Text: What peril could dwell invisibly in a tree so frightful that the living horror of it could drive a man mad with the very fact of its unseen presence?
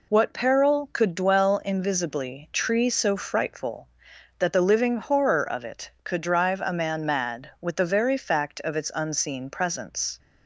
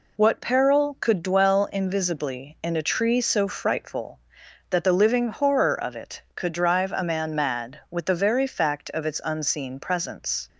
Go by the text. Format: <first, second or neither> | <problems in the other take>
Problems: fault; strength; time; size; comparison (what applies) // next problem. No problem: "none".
second | skips "in a"; at 2.5 s